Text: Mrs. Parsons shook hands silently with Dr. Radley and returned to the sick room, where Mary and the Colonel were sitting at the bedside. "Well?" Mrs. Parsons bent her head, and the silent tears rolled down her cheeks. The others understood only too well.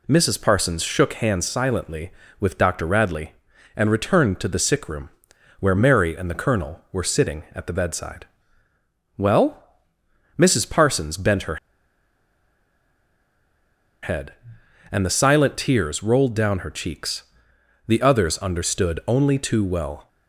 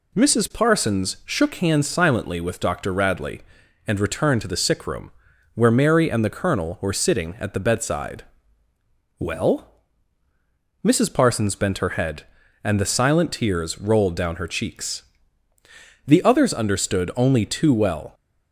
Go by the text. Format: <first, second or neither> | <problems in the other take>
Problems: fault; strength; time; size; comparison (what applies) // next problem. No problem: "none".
second | pauses between "her" and "head"; strong; at 11.5 s; 2.4 s long